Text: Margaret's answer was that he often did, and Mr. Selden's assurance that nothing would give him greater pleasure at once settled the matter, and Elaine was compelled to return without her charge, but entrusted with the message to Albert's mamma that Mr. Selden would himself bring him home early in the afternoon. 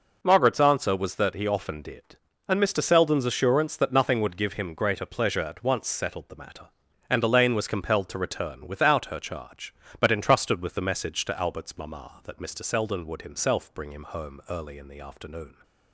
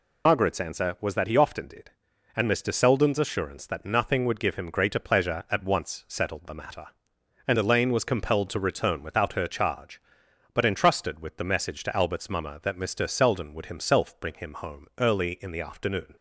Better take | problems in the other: first | loses the start of "Margaret's"; at 0.2 s; 80 ms

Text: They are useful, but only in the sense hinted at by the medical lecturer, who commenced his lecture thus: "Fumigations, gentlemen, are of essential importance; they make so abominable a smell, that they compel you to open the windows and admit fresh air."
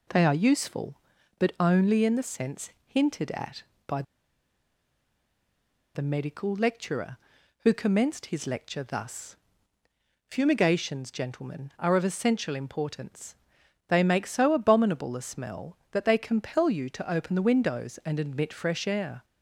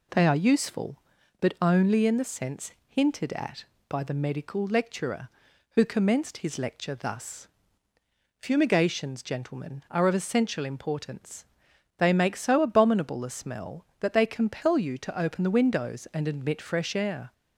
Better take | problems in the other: second | pauses between "sense" and "hinted"; slight; at 2.7 s; 0.16 s long; slight in the second // pauses between "by" and "the"; strong; at 4.0 s; 1.9 s long

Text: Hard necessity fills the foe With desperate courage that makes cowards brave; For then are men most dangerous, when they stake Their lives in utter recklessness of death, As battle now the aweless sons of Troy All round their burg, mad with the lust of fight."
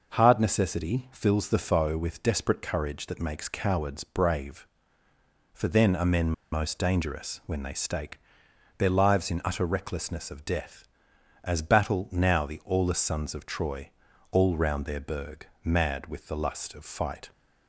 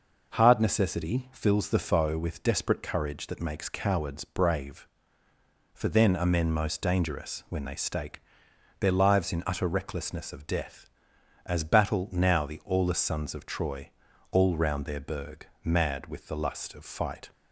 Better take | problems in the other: second | pauses between "men" and "most"; slight; at 6.3 s; 0.20 s long // pauses between "stake" and "Their"; noticeable; at 8.1 s; 0.58 s long; noticeable in the second // pauses between "Troy" and "All"; at 13.8 s; 0.42 s long; also in the second

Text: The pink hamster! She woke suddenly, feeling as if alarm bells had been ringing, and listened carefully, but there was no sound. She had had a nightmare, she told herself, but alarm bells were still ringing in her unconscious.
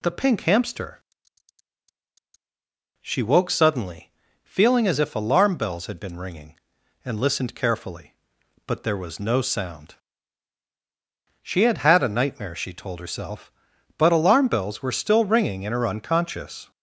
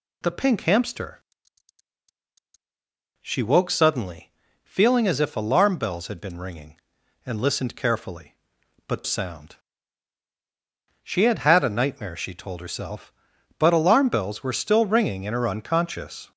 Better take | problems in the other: first | skips "there was no"; at 9.0 s

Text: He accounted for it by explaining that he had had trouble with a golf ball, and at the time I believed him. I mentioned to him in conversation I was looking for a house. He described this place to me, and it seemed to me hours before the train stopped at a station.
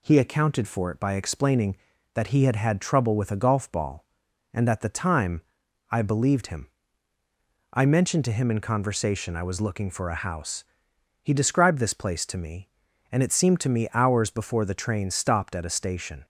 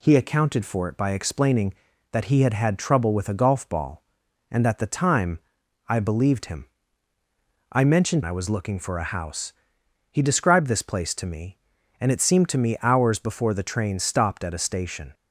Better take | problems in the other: first | pauses between "time" and "I"; noticeable; at 5.3 s; 0.50 s long; noticeable in the first // skips "to him in conversation"; at 8.2 s

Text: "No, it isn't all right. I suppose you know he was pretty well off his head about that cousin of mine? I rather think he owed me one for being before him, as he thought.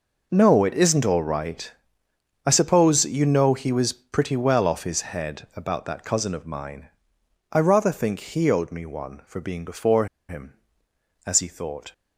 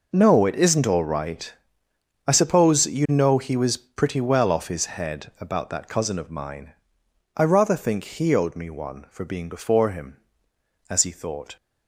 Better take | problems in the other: second | pauses between "before" and "him"; slight; at 10.0 s; 0.23 s long

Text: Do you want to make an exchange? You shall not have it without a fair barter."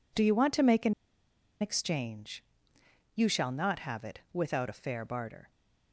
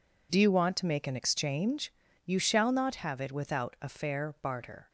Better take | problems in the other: second | pauses between "an" and "exchange"; noticeable; at 0.9 s; 0.67 s long

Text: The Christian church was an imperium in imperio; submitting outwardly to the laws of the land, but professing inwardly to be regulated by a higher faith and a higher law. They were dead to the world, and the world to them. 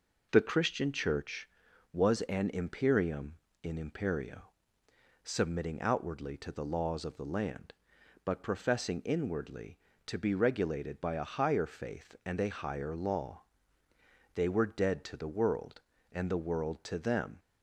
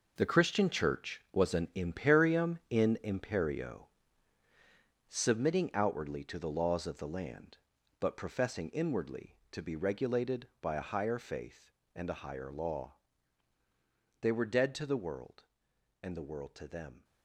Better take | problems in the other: first | gets quieter; strong; throughout; 11.5 dB

